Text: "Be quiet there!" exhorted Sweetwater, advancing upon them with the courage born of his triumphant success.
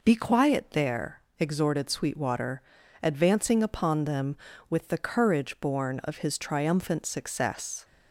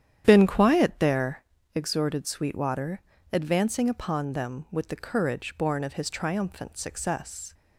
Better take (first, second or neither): first